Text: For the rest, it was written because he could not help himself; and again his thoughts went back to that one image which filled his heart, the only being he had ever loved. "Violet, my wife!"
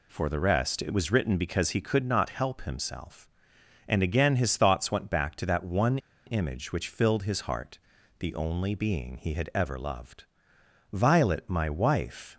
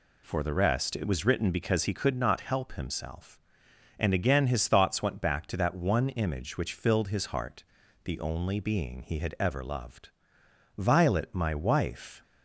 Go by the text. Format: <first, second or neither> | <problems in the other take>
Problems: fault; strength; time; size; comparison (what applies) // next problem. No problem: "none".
second | pauses between "one" and "image"; slight; at 5.9 s; 0.28 s long